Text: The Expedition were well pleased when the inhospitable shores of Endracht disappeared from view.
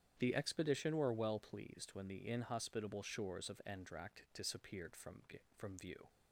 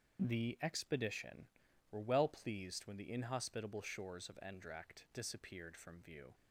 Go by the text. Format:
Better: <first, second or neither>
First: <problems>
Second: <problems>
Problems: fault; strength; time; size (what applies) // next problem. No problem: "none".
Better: second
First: starts louder than the rest; strong; until 1.1 s; 9 dB // says "from" twice; at 5.5 s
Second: starts louder than the rest; strong; until 1.2 s; 7 dB